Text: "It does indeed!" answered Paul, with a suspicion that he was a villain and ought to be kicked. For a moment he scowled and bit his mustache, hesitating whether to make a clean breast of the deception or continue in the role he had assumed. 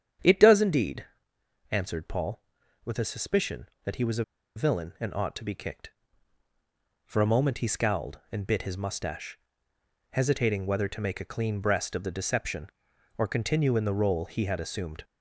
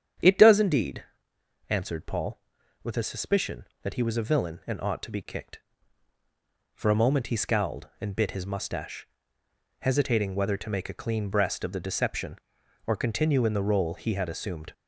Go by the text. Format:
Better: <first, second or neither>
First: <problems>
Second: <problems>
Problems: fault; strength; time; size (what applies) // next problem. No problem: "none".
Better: second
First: starts louder than the rest; strong; until 1.8 s; 8.5 dB // pauses between "a" and "villain"; slight; at 4.2 s; 0.31 s long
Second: starts louder than the rest; strong; until 1.8 s; 8.5 dB